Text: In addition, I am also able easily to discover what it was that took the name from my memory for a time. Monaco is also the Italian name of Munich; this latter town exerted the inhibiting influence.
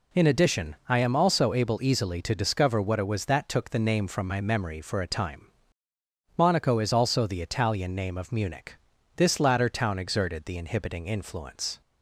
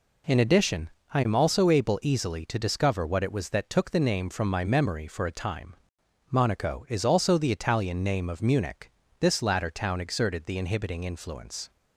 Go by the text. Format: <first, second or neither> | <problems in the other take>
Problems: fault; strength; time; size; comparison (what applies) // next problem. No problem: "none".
neither | none